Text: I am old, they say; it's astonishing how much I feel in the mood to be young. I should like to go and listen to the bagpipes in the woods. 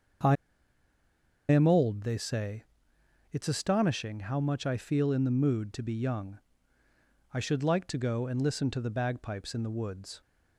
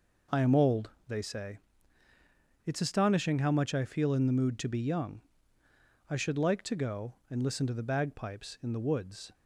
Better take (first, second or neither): second